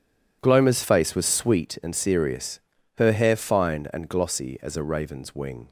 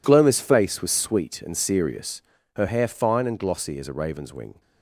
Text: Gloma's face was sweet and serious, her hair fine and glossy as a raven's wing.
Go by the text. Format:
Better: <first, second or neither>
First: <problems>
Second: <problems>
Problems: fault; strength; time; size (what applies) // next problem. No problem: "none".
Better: neither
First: none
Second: none